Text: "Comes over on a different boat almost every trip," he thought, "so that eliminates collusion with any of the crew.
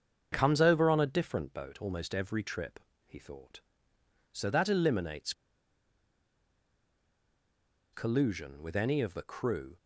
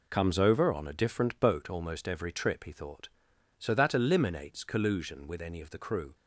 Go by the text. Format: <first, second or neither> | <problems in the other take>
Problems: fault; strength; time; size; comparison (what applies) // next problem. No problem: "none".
second | starts louder than the rest; until 1.3 s; 7 dB // pauses between "eliminates" and "collusion"; strong; at 5.3 s; 2.6 s long